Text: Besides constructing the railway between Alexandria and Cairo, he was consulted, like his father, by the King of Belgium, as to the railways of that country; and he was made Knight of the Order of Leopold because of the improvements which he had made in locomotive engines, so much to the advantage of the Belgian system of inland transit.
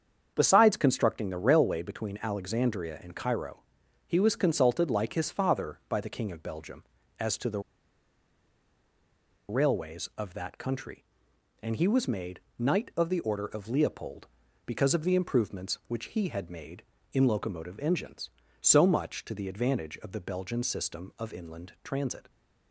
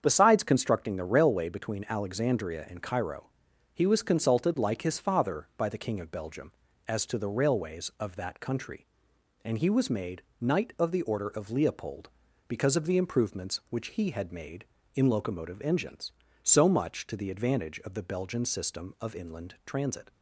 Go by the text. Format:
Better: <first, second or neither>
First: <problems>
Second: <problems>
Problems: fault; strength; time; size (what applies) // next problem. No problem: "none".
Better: second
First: starts louder than the rest; strong; until 1.3 s; 7.5 dB // pauses between "the" and "railways"; strong; at 7.5 s; 1.8 s long // pauses between "made" and "Knight"; slight; at 12.3 s; 0.18 s long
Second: starts louder than the rest; strong; until 1.0 s; 7.5 dB // pauses between "made" and "Knight"; slight; at 10.2 s; 0.18 s long